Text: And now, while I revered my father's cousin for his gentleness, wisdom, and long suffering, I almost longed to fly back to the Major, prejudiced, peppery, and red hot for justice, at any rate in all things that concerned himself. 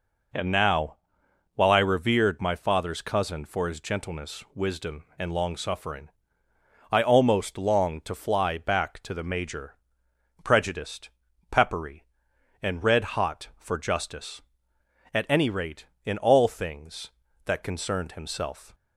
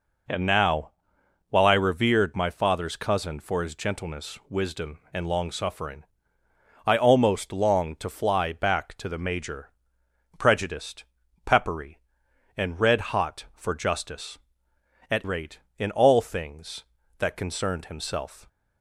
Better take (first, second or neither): first